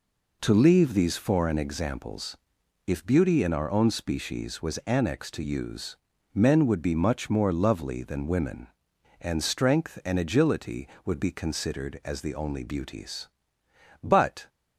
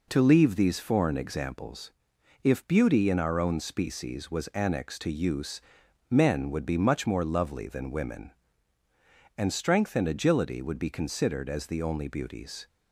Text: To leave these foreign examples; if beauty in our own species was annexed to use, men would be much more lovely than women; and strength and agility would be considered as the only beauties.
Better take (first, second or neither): second